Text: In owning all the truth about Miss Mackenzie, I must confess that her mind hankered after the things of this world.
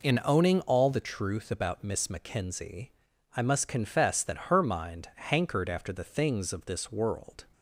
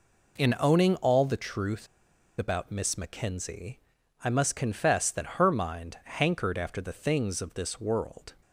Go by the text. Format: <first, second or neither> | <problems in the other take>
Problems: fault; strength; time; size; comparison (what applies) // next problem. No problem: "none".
first | pauses between "truth" and "about"; noticeable; at 1.8 s; 0.53 s long